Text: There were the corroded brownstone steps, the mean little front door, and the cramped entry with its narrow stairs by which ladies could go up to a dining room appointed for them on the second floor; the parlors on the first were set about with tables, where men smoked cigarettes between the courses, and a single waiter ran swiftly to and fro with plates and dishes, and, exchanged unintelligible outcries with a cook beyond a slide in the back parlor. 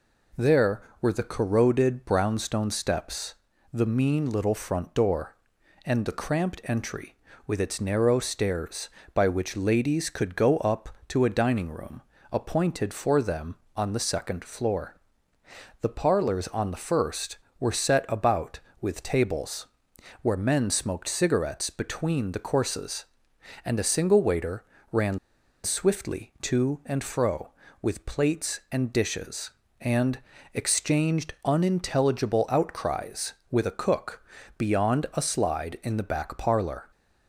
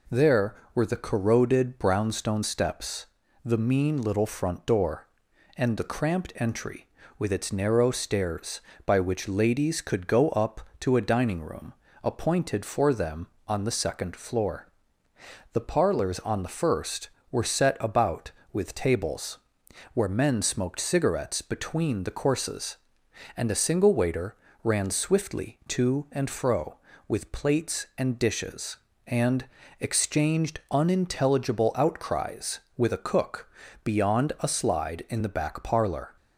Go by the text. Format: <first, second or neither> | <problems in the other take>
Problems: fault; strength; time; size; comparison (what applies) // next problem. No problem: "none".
second | pauses between "room" and "appointed"; slight; at 12.0 s; 0.30 s long; slight in the second // pauses between "waiter" and "ran"; slight; at 24.6 s; 0.28 s long; slight in the second // pauses between "ran" and "swiftly"; noticeable; at 25.1 s; 0.45 s long // pauses between "cook" and "beyond"; slight; at 34.2 s; 0.36 s long; slight in the second